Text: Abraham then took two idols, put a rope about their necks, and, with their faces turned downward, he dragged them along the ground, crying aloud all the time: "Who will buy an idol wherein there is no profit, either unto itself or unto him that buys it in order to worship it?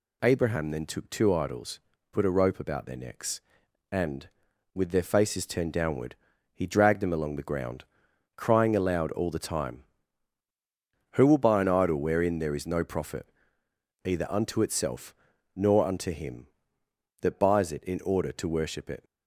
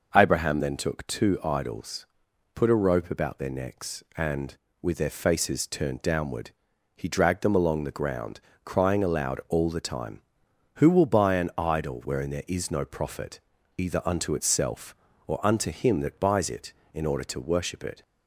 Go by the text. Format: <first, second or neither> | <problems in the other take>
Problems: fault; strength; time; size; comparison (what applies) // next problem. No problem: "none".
second | says "nor" for "or"; at 15.5 s